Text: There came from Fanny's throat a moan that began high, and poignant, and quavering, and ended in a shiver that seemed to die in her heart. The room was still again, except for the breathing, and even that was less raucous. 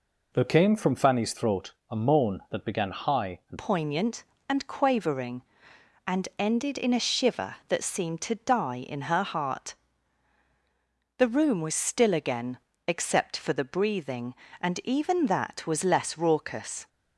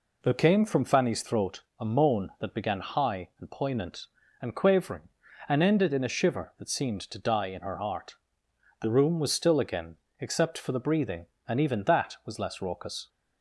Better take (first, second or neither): second